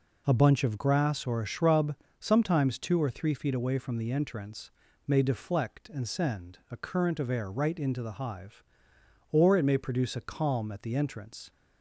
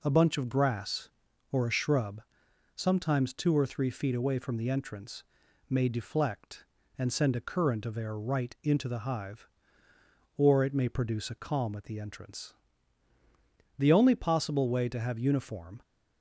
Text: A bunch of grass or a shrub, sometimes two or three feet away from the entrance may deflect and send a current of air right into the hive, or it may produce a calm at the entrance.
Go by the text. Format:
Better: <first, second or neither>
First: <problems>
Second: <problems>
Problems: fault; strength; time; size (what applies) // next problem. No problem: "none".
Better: first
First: pauses between "entrance" and "may"; slight; at 4.7 s; 0.36 s long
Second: pauses between "entrance" and "may"; noticeable; at 5.2 s; 0.46 s long // goes on to say "The only possible way to have uniform"; strong; from 13.7 s on; 2.0 s long